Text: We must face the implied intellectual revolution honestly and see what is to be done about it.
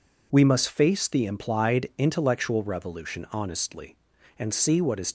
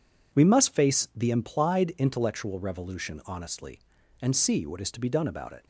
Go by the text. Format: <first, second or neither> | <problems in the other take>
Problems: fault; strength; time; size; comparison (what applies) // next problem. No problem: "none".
second | stops before "to be done about it"; at 5.0 s